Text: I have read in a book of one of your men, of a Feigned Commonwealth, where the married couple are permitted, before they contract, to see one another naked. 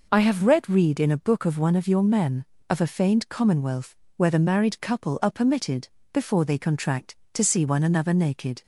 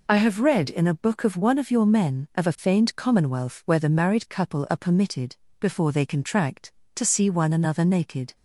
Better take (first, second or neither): second